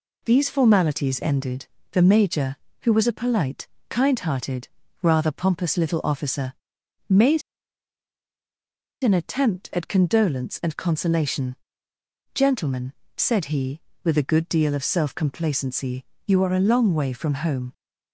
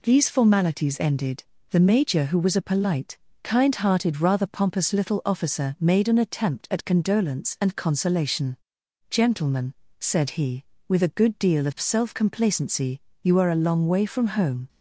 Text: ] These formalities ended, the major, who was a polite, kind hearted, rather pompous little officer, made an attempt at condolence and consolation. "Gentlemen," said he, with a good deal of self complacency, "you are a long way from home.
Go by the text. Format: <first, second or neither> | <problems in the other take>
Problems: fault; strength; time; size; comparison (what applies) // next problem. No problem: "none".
second | pauses between "made" and "an"; strong; at 7.4 s; 1.6 s long